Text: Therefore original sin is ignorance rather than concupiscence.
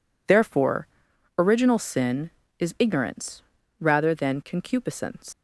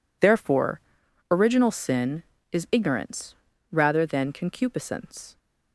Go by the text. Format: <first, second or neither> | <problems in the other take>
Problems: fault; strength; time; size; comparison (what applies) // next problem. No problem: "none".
second | pauses between "Therefore" and "original"; noticeable; at 0.8 s; 0.50 s long; noticeable in the second // pauses between "ignorance" and "rather"; slight; at 3.4 s; 0.36 s long; slight in the second // leaves "concupiscence" unfinished; at 5.3 s; 160 ms